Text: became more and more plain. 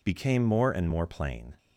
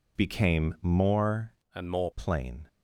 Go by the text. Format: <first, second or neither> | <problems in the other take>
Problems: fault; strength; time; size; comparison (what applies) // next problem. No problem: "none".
first | changes voice from "and" to "more"; from 1.7 to 2.1 s; 0.4 s long